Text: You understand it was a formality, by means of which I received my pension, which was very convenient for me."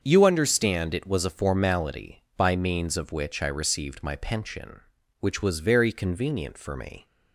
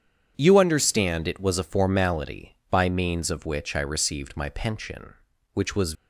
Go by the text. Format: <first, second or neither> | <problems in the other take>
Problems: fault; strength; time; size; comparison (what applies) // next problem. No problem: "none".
first | starts louder than the rest; strong; until 1.3 s; 8 dB; also in the first // stops before "very convenient for me"; at 5.9 s